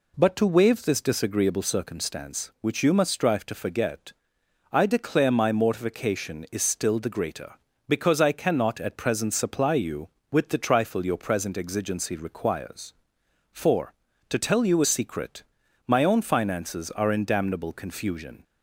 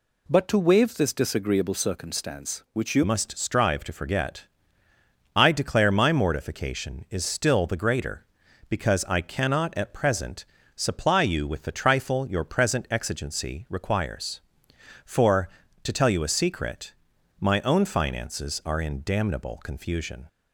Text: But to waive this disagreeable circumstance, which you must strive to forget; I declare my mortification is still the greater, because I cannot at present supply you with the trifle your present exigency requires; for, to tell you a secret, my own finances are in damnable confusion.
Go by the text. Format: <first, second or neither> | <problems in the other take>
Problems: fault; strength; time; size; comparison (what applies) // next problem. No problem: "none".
first | changes voice at "must"; from 3.0 s on; 17.2 s long // pauses between "present" and "supply"; slight; at 10.4 s; 0.32 s long